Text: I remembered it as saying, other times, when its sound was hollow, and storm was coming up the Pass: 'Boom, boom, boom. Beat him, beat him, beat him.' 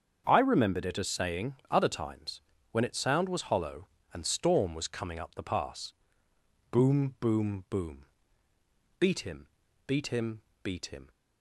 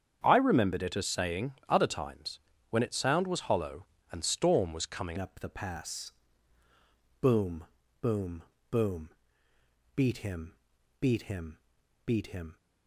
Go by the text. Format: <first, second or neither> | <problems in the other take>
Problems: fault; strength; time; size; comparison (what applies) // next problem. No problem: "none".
first | starts louder than the rest; strong; until 1.2 s; 8 dB; strong in the first // changes voice at "up"; from 5.1 s on; 7.4 s long